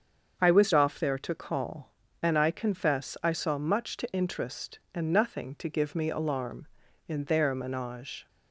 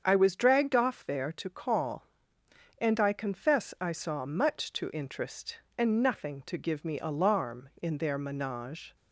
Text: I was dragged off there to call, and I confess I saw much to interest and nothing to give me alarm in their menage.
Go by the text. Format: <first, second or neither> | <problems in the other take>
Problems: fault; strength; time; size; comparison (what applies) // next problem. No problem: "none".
second | starts louder than the rest; until 1.4 s; 7 dB; strong in the second // skips "dragged"; at 0.7 s